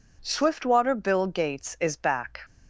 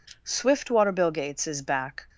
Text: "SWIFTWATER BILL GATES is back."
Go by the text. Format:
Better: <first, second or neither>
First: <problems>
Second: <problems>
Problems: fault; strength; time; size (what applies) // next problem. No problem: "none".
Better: neither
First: none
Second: none